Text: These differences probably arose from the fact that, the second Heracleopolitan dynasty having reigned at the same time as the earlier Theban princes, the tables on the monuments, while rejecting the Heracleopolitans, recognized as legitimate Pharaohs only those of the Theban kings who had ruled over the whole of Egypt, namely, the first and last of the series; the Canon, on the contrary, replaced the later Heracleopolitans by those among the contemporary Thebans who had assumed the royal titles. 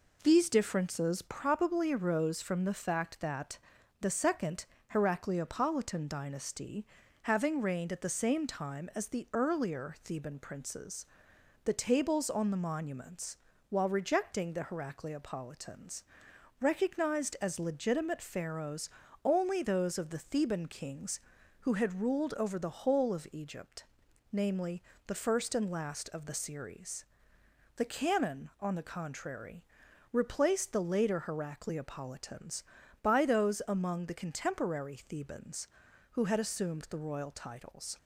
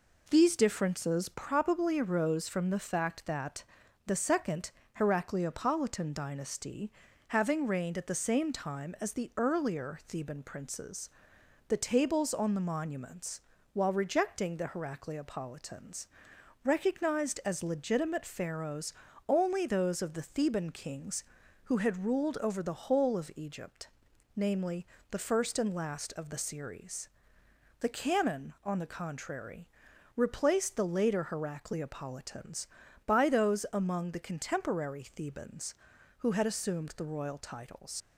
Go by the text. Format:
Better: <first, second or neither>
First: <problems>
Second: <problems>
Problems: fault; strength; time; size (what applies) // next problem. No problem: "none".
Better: first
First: pauses between "second" and "Heracleopolitan"; slight; at 4.6 s; 0.28 s long // pauses between "dynasty" and "having"; slight; at 6.8 s; 0.36 s long // pauses between "Pharaohs" and "only"; slight; at 18.8 s; 0.34 s long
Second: pauses between "second" and "Heracleopolitan"; slight; at 4.6 s; 0.28 s long // pauses between "dynasty" and "having"; slight; at 6.9 s; 0.36 s long // pauses between "Pharaohs" and "only"; slight; at 18.9 s; 0.34 s long // leaves "titles" unfinished; at 38.0 s; 40 ms